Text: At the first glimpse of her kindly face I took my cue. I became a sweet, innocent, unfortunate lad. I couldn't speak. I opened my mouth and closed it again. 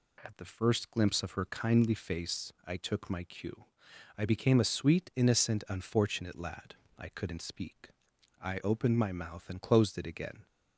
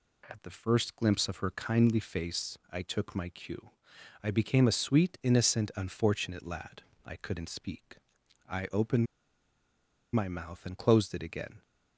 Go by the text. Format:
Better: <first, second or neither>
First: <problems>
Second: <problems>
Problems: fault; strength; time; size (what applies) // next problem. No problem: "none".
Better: first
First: pauses between "face" and "I"; slight; at 2.5 s; 0.16 s long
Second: pauses between "face" and "I"; slight; at 2.5 s; 0.16 s long // pauses between "opened" and "my"; at 9.0 s; 1.0 s long